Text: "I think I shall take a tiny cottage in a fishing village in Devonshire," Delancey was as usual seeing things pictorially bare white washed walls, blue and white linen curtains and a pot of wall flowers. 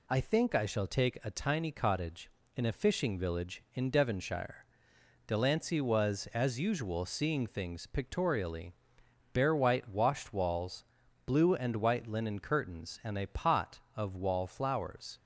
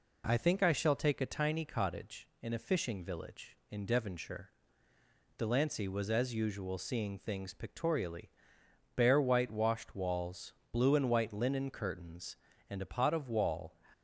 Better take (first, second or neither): first